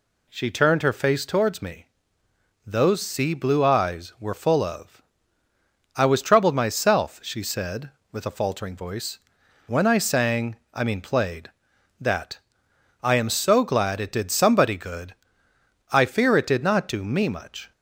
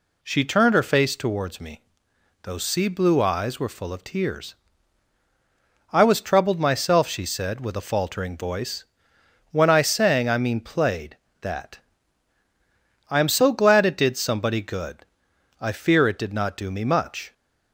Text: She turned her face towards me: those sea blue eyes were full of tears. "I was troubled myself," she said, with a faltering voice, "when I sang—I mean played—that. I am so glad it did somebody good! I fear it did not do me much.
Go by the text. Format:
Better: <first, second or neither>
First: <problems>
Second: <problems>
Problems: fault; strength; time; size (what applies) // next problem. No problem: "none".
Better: second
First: skips "tears"; at 5.4 s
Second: none